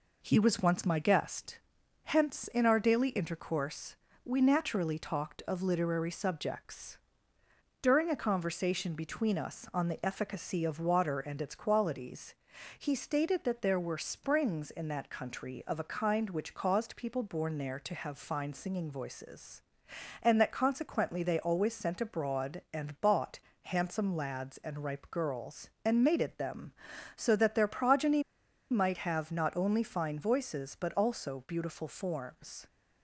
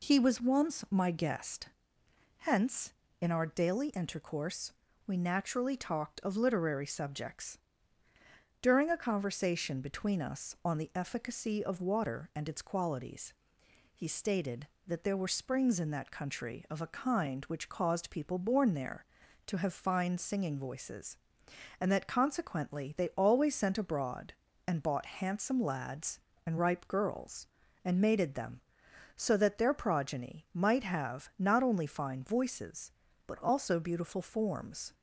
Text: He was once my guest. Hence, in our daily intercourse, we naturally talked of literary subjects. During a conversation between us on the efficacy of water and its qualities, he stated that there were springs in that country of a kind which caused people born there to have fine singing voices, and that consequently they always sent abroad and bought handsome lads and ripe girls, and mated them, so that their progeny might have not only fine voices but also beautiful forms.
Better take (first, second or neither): second